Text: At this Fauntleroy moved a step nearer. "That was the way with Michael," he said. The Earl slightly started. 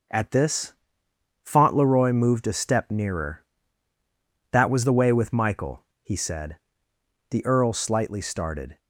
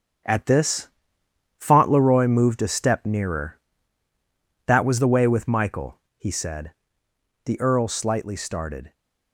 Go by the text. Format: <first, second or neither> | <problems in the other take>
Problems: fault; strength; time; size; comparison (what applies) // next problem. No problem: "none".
first | gets quieter; strong; throughout; 9 dB // pauses between "this" and "Fauntleroy"; noticeable; at 0.8 s; 0.72 s long; noticeable in the first